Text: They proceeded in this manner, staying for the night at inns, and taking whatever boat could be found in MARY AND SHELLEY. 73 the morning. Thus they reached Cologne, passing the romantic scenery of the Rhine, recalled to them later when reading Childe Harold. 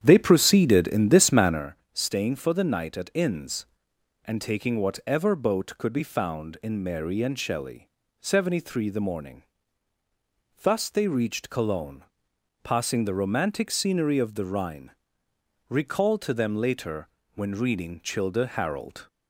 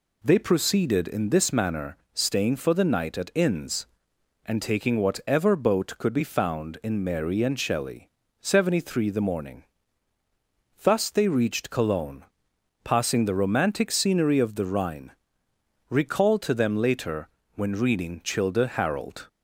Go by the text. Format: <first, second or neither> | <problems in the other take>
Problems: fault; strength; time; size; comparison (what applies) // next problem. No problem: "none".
second | starts louder than the rest; strong; until 1.7 s; 9 dB // pauses between "later" and "when"; slight; at 17.0 s; 0.28 s long; slight in the second